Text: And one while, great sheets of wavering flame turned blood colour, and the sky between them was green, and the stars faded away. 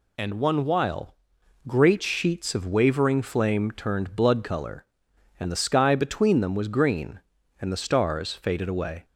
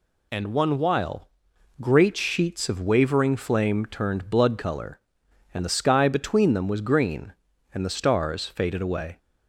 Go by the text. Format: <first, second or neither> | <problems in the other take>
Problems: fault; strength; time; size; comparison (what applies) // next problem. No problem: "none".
neither | none